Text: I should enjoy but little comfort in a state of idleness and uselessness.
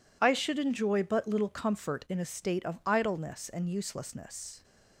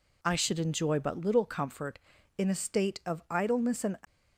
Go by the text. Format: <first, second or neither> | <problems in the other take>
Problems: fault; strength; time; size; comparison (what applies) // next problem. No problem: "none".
first | stops before "uselessness"; at 4.0 s